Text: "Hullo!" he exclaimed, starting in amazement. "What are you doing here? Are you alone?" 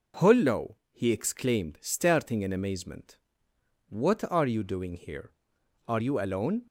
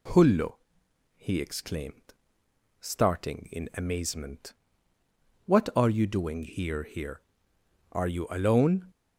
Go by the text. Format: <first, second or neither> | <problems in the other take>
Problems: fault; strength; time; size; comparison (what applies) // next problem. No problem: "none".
first | says "here" twice; at 6.8 s